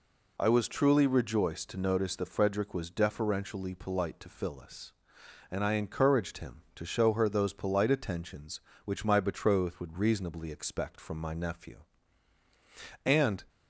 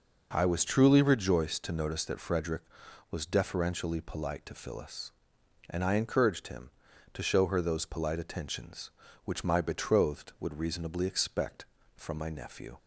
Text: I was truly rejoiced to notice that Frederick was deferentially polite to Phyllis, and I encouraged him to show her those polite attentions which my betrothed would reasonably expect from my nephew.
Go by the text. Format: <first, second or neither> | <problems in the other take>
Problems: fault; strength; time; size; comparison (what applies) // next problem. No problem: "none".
second | goes on to say "And"; slight; from 13.0 s on; 0.40 s long